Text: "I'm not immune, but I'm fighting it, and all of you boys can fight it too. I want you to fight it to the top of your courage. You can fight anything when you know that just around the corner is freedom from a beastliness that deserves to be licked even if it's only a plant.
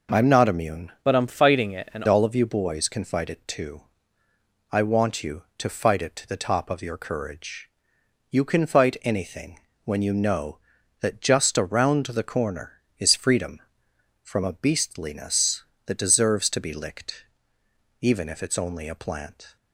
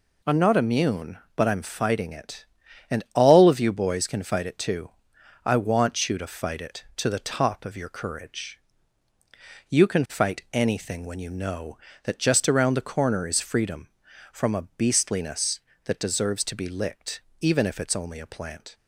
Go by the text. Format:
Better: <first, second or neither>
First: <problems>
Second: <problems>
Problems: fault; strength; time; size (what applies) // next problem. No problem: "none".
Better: second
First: changes voice from "but" to "and"; from 1.0 to 2.0 s; 1.0 s long // pauses between "anything" and "when"; slight; at 9.5 s; 0.26 s long // pauses between "licked" and "even"; noticeable; at 17.2 s; 0.78 s long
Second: pauses between "licked" and "even"; slight; at 17.2 s; 0.20 s long